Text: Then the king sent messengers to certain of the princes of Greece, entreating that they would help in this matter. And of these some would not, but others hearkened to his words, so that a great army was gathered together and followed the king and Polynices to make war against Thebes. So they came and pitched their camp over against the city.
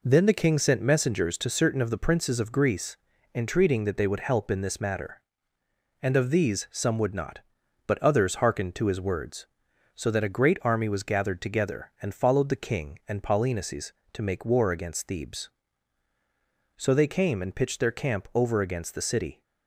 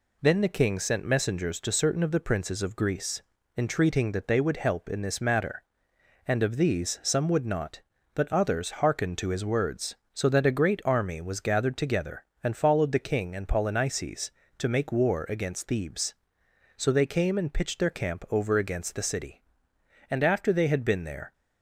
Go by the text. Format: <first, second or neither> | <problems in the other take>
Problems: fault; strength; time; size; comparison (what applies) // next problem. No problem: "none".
first | goes on to say "And after they had been there"; noticeable; from 20.0 s on; 1.2 s long